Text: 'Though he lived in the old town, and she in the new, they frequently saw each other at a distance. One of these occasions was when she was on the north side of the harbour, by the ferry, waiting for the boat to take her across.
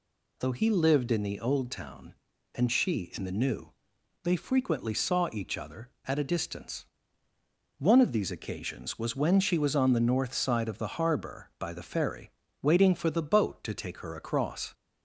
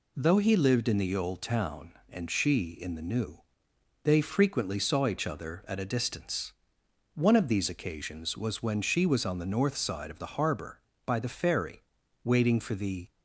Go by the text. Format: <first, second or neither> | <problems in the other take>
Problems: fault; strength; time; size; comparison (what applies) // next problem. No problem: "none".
first | stops before "boat to take her across"; at 13.0 s